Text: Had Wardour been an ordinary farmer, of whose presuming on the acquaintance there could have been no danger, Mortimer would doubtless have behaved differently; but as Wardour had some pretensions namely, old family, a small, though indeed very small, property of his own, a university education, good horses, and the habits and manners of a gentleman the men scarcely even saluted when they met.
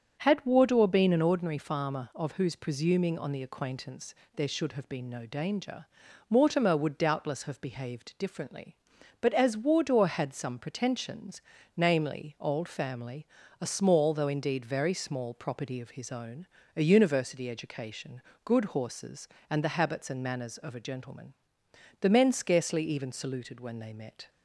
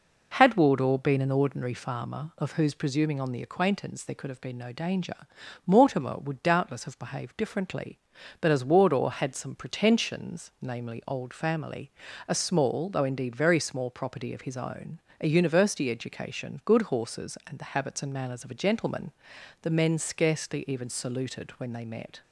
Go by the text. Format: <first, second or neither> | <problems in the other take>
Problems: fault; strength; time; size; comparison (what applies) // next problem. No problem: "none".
second | starts louder than the rest; strong; until 1.2 s; 7.5 dB // pauses between "acquaintance" and "there"; slight; at 4.1 s; 0.18 s long // says "should" for "could"; at 4.4 s // pauses between "pretensions" and "namely"; slight; at 11.3 s; 0.36 s long // pauses between "gentleman" and "the"; noticeable; at 21.3 s; 0.66 s long; noticeable in the second